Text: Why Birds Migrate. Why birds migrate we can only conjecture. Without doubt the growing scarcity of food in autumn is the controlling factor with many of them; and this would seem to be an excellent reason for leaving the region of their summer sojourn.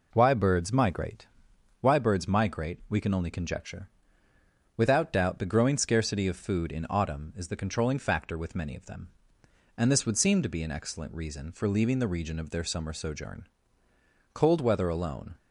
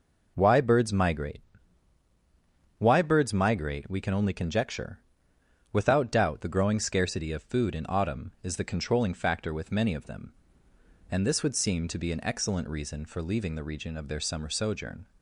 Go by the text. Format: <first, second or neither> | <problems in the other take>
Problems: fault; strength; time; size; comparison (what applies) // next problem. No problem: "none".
second | goes on to say "Cold weather alone"; noticeable; from 14.3 s on; 1.0 s long